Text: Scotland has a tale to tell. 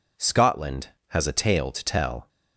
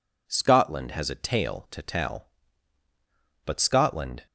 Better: first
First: none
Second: goes on to say "But Scotland"; noticeable; from 3.4 s on; 0.80 s long

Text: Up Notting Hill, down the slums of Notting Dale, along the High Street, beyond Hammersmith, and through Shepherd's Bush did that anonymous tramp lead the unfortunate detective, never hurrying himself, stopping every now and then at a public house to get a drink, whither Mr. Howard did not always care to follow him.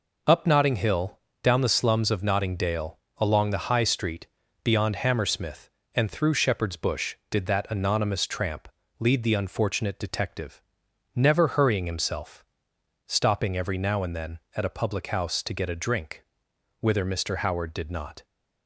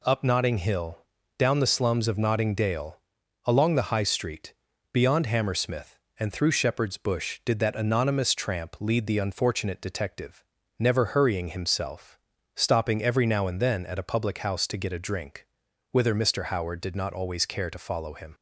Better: second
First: pauses between "tramp" and "lead"; slight; at 8.6 s; 0.28 s long // stops before "always care to follow him"; at 18.2 s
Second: none

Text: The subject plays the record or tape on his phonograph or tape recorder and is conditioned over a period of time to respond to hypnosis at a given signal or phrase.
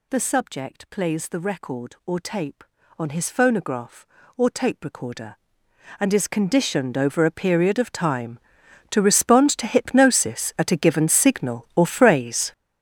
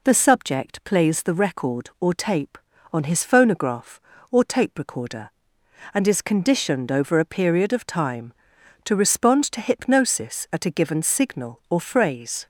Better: second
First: gets louder; strong; throughout; 13 dB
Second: none

